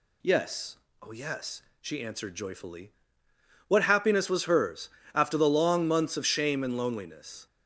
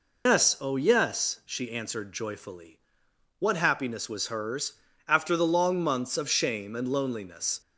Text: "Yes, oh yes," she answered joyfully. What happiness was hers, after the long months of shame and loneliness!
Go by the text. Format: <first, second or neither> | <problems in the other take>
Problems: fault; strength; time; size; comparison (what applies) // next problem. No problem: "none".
first | loses the start of "Yes"; at 0.2 s; 125 ms